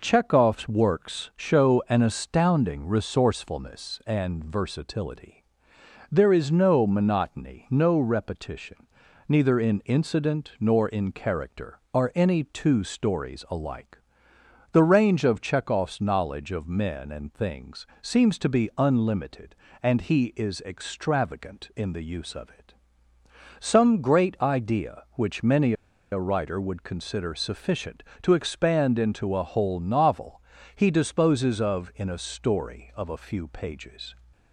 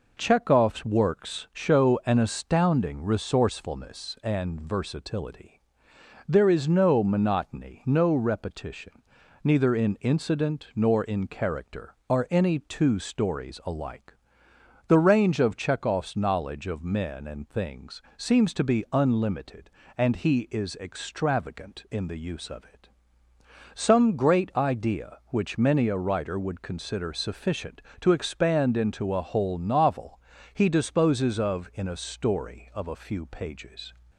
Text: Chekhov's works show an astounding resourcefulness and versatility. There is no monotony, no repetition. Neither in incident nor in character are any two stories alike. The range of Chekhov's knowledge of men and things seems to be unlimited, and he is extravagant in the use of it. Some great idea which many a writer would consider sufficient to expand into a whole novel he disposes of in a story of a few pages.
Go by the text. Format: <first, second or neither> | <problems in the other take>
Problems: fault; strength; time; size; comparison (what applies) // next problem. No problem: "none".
second | pauses between "things" and "seems"; slight; at 17.8 s; 0.16 s long; slight in the second // pauses between "many" and "a"; at 25.7 s; 0.38 s long // pauses between "novel" and "he"; slight; at 30.3 s; 0.36 s long; slight in the second